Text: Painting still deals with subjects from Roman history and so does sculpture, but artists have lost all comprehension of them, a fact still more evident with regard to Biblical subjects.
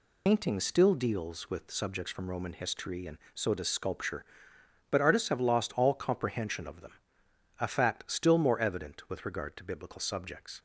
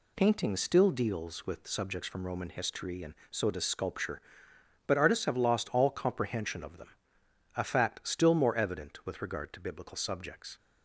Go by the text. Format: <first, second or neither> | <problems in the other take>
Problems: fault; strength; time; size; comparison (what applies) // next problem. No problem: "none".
second | loses the start of "Painting"; at 0.2 s; 60 ms